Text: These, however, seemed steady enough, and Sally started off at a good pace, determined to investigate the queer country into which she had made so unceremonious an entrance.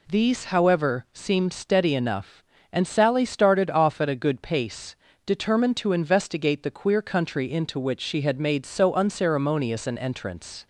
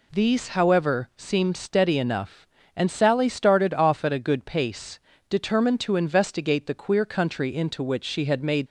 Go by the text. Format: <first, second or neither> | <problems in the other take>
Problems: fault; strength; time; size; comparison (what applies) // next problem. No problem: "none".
first | stops before "so unceremonious an entrance"; at 8.6 s